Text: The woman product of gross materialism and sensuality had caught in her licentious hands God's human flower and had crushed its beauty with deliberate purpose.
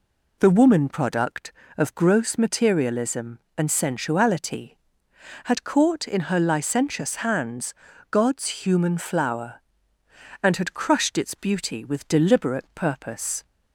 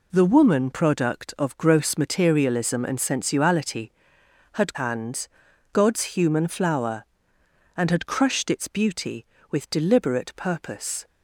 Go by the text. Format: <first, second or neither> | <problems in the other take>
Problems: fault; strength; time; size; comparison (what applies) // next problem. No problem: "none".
first | skips "caught in her licentious"; at 4.7 s // pauses between "hands" and "God's"; noticeable; at 5.2 s; 0.46 s long; also in the first